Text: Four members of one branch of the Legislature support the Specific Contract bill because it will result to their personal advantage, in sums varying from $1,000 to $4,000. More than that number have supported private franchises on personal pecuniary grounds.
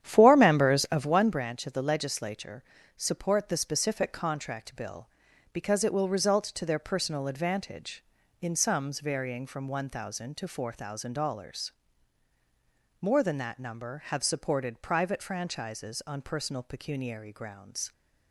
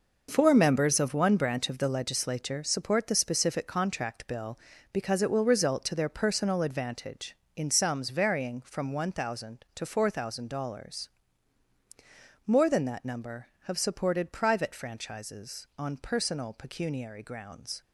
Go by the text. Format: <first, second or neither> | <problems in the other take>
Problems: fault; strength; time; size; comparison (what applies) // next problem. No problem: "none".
second | starts louder than the rest; strong; until 1.2 s; 10 dB // pauses between "Legislature" and "support"; slight; at 2.6 s; 0.34 s long